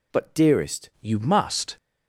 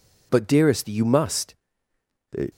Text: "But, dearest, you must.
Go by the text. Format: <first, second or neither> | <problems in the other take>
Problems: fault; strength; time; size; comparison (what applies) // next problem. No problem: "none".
second | changes voice at "you"; from 1.0 s on; 0.7 s long